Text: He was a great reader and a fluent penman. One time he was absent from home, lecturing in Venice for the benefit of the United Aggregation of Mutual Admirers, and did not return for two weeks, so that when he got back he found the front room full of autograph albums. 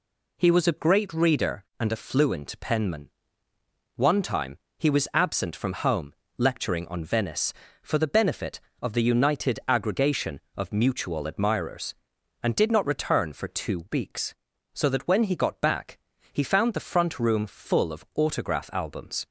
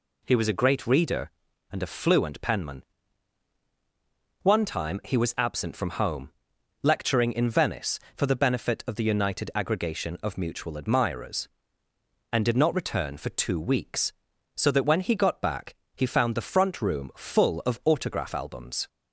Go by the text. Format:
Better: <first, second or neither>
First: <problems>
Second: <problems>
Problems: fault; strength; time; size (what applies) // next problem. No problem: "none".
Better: second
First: pauses between "time" and "he"; slight; at 4.5 s; 0.20 s long // says "on" for "in"; at 6.8 s // pauses between "back" and "he"; slight; at 15.9 s; 0.36 s long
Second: pauses between "back" and "he"; slight; at 15.7 s; 0.20 s long